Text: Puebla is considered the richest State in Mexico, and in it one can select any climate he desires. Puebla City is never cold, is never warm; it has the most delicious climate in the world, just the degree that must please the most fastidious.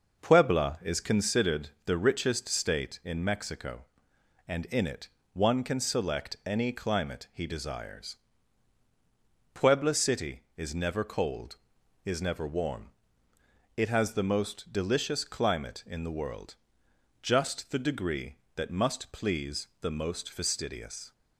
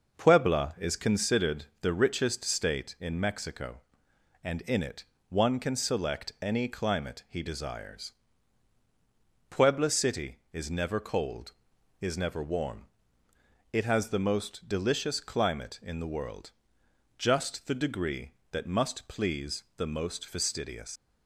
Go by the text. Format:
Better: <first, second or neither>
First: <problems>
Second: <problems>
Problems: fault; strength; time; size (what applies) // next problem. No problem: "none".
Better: first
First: pauses between "considered" and "the"; slight; at 1.7 s; 0.16 s long // pauses between "it" and "one"; slight; at 5.0 s; 0.24 s long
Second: pauses between "considered" and "the"; slight; at 1.6 s; 0.16 s long // pauses between "it" and "one"; slight; at 5.0 s; 0.24 s long // leaves "fastidious" unfinished; at 20.9 s; 125 ms